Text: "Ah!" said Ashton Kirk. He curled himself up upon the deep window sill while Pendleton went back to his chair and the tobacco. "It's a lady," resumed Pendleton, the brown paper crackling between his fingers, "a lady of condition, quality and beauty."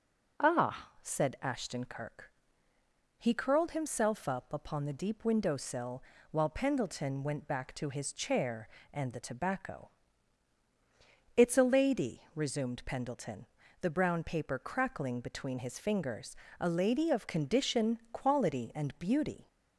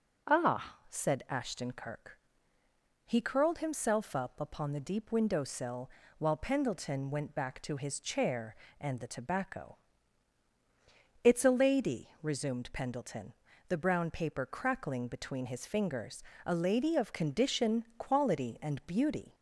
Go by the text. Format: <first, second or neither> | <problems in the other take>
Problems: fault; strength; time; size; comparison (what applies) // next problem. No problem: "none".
neither | pauses between "sill" and "while"; slight; the same in both